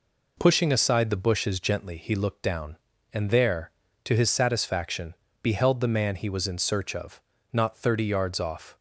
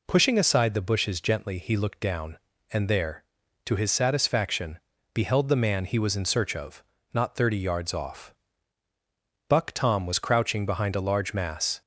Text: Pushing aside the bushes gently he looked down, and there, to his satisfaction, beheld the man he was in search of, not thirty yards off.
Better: first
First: none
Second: goes on to say "Buck Tom was crouching behind a large mass"; strong; from 9.4 s on; 2.3 s long

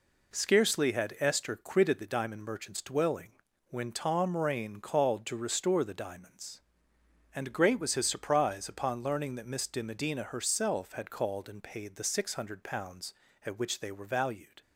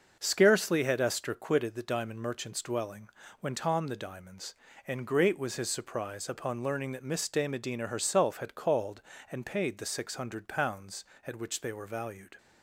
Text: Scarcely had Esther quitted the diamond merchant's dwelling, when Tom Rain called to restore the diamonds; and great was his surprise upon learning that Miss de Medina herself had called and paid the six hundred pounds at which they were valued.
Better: first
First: none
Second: starts louder than the rest; noticeable; until 1.2 s; 6 dB // skips "Rain called to restore"; at 3.8 s

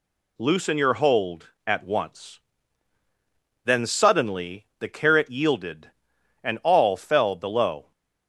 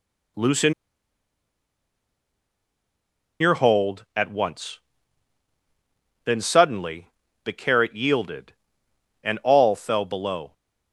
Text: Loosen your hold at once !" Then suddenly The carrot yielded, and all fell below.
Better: first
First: none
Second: pauses between "Loosen" and "your"; strong; at 0.7 s; 2.6 s long // pauses between "suddenly" and "The"; slight; at 7.0 s; 0.36 s long

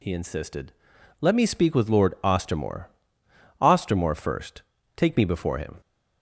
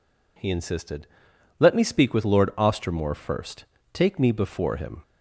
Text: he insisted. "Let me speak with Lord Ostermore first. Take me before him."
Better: second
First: says "Ostermore" twice; at 3.6 s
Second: none

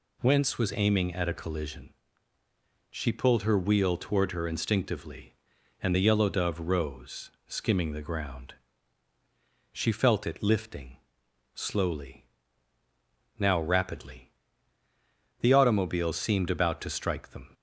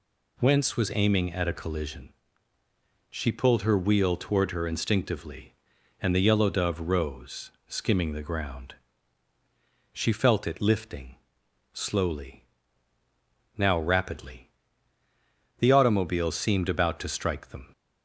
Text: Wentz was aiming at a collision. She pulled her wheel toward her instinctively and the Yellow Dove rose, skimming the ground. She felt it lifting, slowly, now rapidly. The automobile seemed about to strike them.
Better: neither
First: none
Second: none

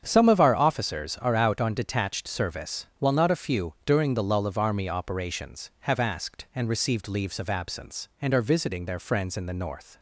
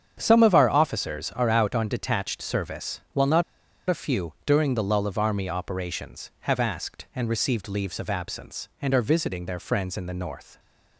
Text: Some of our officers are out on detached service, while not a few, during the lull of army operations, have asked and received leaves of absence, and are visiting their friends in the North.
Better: first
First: starts louder than the rest; strong; until 1.0 s; 8 dB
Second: starts louder than the rest; strong; until 1.2 s; 8 dB // pauses between "not" and "a"; at 3.4 s; 0.45 s long

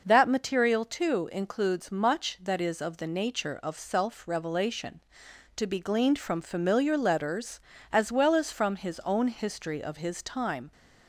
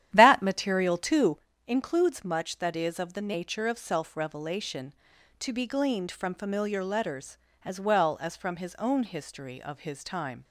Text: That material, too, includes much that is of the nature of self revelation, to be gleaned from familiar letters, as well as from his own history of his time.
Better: first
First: none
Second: starts louder than the rest; strong; until 1.4 s; 11 dB

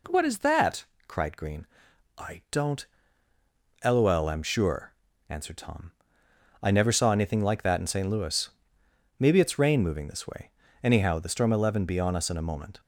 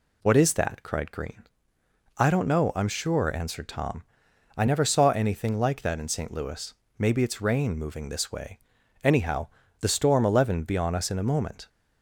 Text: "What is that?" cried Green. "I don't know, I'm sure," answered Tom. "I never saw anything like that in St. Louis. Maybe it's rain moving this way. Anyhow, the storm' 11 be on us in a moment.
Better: second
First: says "lol" for "know"; at 3.8 s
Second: none

